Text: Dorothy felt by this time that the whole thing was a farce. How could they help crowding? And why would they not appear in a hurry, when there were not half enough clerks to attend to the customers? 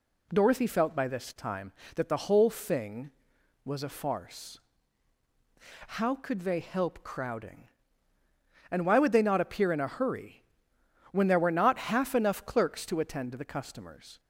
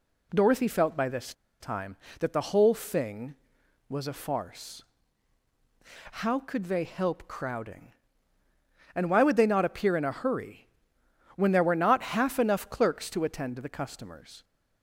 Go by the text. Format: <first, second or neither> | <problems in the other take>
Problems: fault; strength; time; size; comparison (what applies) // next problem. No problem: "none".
first | pauses between "this" and "time"; slight; at 1.3 s; 0.27 s long